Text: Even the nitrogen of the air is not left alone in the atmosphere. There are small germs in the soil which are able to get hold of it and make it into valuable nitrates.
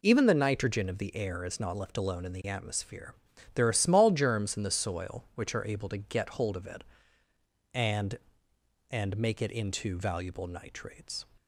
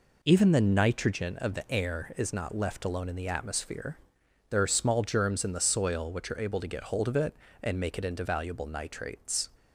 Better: second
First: says "and" twice; at 8.9 s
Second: none

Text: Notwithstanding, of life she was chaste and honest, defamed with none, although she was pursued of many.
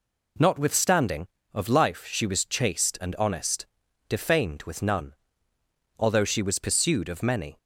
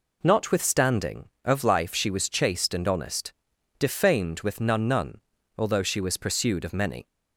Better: first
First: none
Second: says "none" twice; at 4.8 s

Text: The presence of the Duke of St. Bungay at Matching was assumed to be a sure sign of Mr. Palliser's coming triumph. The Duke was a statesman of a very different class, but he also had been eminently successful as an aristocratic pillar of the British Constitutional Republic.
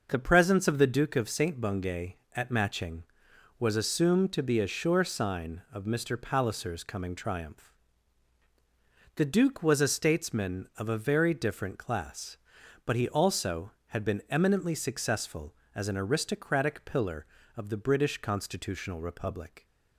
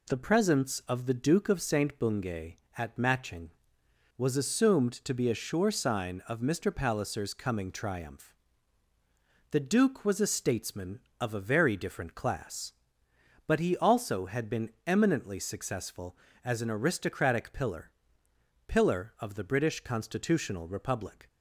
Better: first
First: none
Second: pauses between "been" and "eminently"; slight; at 14.6 s; 0.16 s long // says "pillar" twice; at 18.6 s

